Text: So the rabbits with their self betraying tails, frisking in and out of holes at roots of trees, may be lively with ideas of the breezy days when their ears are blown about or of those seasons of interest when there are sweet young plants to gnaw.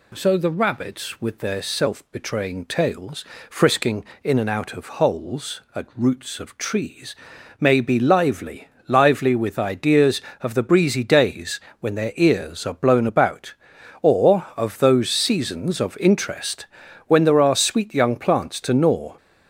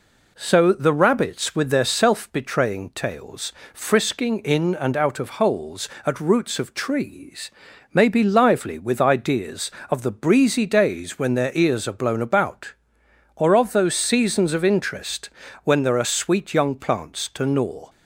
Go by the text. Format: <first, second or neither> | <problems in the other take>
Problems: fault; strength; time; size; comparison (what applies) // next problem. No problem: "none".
second | says "lively" twice; at 8.8 s // pauses between "days" and "when"; slight; at 11.6 s; 0.18 s long // pauses between "interest" and "when"; at 16.6 s; 0.40 s long; slight in the second